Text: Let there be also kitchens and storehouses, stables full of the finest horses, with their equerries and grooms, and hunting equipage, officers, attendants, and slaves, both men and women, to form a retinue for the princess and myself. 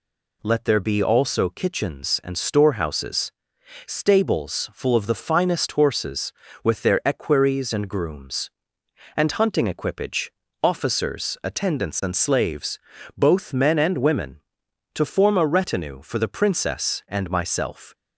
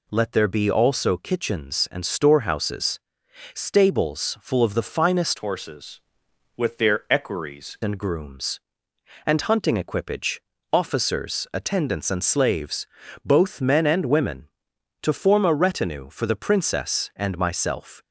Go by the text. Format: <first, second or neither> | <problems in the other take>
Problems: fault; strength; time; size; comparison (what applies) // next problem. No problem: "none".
first | changes voice from "horses" to "equerries"; from 5.3 to 7.7 s; 2.4 s long